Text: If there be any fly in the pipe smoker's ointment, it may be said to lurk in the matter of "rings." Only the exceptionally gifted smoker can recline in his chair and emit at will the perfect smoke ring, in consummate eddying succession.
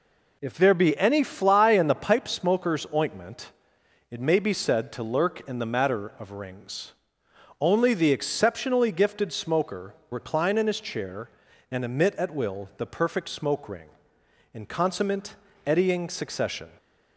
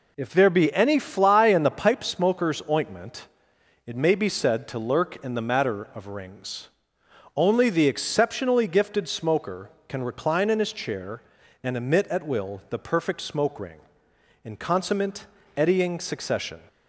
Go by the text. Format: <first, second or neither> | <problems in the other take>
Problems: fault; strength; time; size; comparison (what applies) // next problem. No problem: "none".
second | skips "can"; at 10.0 s // pauses between "consummate" and "eddying"; slight; at 15.3 s; 0.32 s long; slight in the second